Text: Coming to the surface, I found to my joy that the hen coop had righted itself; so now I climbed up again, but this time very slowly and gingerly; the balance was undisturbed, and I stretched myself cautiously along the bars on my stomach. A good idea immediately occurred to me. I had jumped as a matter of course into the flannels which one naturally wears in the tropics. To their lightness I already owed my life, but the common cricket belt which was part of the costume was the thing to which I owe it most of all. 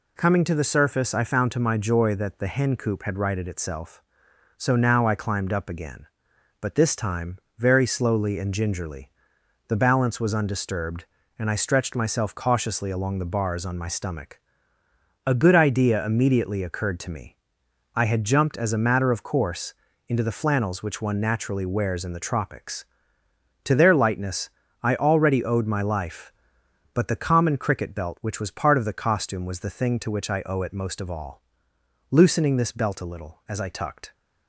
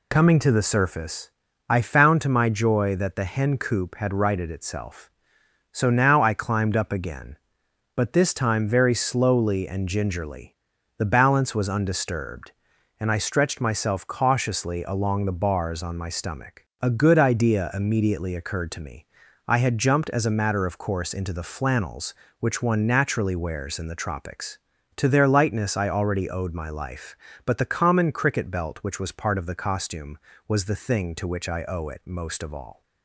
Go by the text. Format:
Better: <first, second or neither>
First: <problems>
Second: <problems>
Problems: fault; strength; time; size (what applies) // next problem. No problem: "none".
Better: second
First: pauses between "time" and "very"; slight; at 7.3 s; 0.22 s long // pauses between "course" and "into"; slight; at 19.7 s; 0.34 s long // pauses between "lightness" and "I"; slight; at 24.4 s; 0.32 s long // goes on to say "Loosening this belt a little as I tucked"; strong; from 32.1 s on; 2.0 s long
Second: none